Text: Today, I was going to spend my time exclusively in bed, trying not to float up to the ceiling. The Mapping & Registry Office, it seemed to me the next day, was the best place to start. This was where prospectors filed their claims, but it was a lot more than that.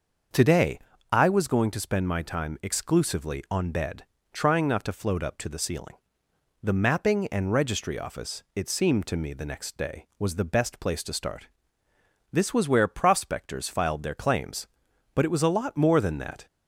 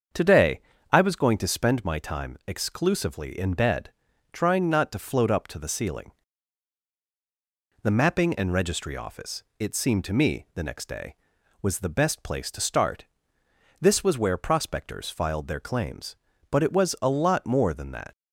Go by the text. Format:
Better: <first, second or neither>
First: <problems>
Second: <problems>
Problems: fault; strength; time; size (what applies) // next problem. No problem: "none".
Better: second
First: starts louder than the rest; until 1.6 s; 6.5 dB // says "on" for "in"; at 3.4 s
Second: starts louder than the rest; until 1.4 s; 7 dB